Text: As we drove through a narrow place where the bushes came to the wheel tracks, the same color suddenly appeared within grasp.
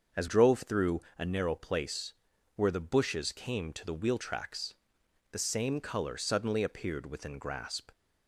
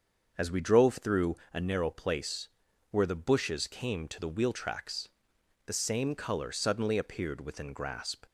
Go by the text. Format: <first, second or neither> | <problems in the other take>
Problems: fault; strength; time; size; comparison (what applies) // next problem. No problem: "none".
second | starts louder than the rest; until 1.3 s; 6.5 dB; also in the second // skips "we"; at 0.2 s // pauses between "through" and "a"; slight; at 1.0 s; 0.16 s long; slight in the second // pauses between "place" and "where"; at 2.1 s; 0.42 s long; also in the second